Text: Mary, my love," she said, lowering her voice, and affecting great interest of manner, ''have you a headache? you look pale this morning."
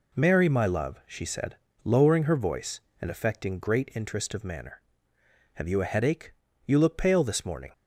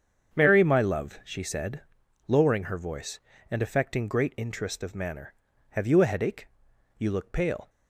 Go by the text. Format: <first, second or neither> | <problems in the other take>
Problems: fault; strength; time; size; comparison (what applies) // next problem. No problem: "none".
first | starts louder than the rest; strong; until 1.4 s; 7 dB // stops before "this morning"; at 7.6 s